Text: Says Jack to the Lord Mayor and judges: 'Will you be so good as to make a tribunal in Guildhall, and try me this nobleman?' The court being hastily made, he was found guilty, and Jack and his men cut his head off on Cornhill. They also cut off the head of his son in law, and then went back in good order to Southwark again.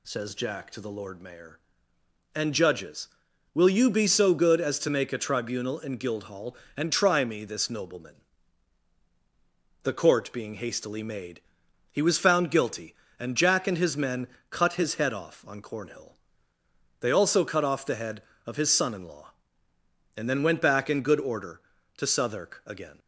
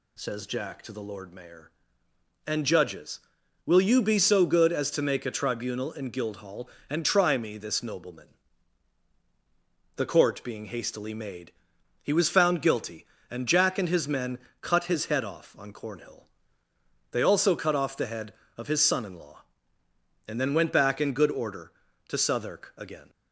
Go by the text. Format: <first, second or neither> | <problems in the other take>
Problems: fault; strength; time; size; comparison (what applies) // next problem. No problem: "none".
neither | pauses between "men" and "cut"; slight; the same in both